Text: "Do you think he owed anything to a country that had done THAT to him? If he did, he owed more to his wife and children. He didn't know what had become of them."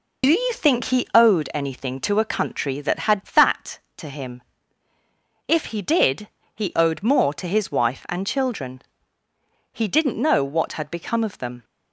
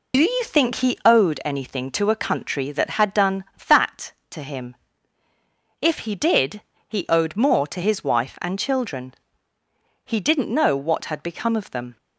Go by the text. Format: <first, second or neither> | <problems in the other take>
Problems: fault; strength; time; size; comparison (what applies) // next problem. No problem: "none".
second | skips "done"; at 3.2 s